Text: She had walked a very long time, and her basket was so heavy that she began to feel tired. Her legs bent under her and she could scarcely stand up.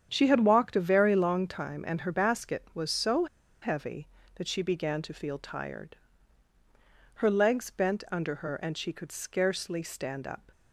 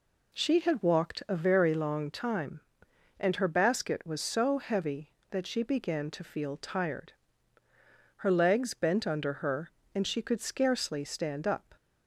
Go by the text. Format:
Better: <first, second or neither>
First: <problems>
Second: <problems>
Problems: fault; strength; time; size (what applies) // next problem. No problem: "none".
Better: second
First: starts louder than the rest; strong; until 1.1 s; 8.5 dB // pauses between "so" and "heavy"; at 3.2 s; 0.36 s long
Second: none